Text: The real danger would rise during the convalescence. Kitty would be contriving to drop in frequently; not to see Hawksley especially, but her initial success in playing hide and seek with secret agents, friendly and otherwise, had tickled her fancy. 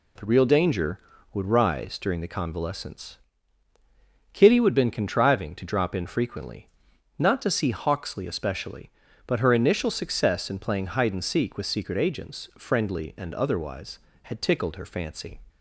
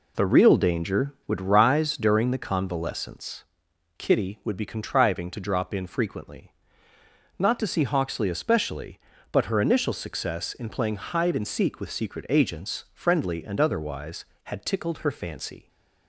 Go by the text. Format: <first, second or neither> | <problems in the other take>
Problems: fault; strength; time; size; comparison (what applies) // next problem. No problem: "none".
second | says "been" for "be"; at 4.7 s